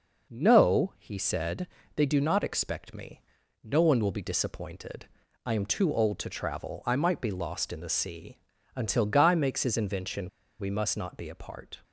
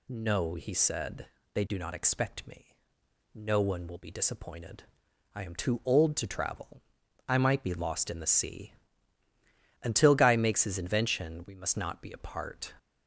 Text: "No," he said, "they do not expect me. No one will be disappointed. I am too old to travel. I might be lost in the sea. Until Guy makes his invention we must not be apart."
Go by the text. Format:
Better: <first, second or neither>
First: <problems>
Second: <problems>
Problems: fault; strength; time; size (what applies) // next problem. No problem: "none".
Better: second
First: pauses between "invention" and "we"; slight; at 10.2 s; 0.31 s long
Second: none